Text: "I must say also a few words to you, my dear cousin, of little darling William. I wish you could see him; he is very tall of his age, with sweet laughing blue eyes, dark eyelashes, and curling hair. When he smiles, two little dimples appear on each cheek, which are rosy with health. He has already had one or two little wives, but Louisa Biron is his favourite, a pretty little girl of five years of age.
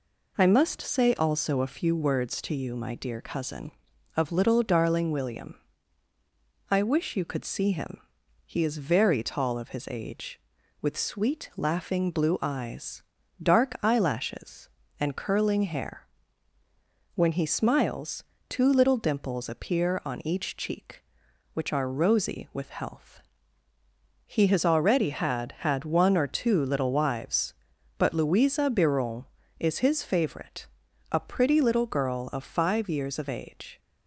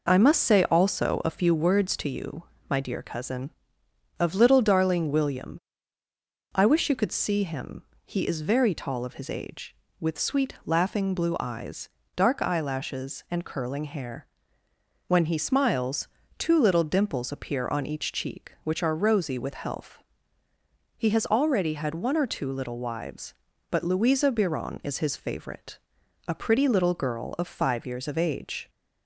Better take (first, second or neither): second